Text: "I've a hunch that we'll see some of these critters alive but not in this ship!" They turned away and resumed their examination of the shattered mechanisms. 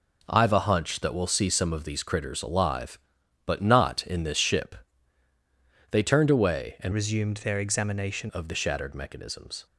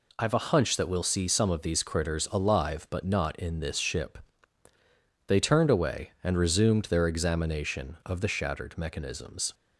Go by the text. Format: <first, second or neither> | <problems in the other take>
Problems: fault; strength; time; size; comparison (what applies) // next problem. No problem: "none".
second | changes voice from "resumed" to "examination"; from 6.9 to 8.2 s; 1.3 s long